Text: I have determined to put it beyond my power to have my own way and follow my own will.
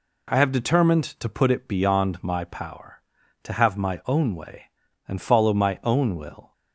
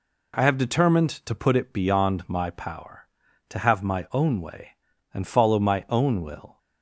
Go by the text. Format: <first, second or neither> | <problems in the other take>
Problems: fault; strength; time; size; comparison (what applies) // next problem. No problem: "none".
neither | none